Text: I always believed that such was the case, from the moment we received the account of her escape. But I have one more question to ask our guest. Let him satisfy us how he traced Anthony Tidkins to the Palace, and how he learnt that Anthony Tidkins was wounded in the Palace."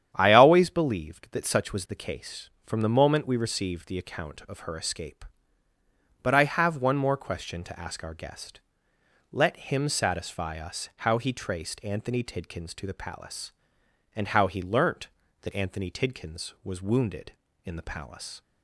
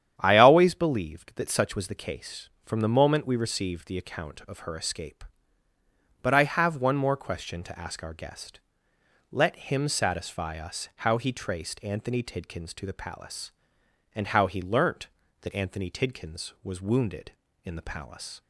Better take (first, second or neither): neither